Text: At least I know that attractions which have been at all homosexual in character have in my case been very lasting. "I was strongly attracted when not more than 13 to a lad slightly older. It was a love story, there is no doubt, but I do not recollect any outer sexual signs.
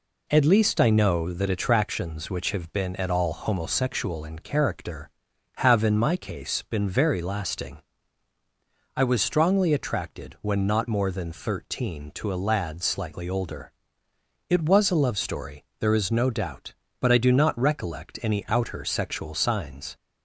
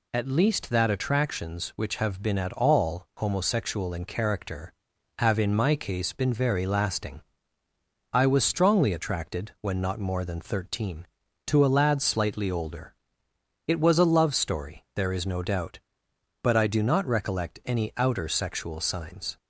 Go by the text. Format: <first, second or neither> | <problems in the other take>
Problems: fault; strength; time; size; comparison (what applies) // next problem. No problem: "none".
first | skips "I know"; at 0.7 s